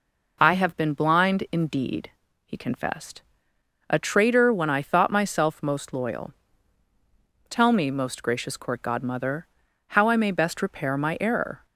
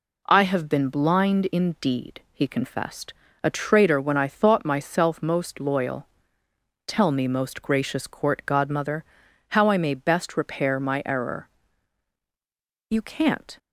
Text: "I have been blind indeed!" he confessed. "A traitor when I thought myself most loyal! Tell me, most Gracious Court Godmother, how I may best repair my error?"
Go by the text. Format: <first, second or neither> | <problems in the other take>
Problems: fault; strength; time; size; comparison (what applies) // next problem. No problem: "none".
first | goes on to say "You can't"; noticeable; from 12.8 s on; 0.70 s long